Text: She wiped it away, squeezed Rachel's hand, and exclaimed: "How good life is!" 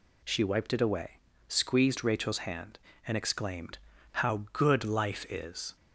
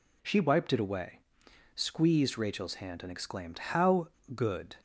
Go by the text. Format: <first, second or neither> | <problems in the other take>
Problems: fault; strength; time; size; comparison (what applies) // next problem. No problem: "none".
first | pauses between "How" and "good"; slight; at 4.0 s; 0.25 s long // stops before "life is"; at 4.7 s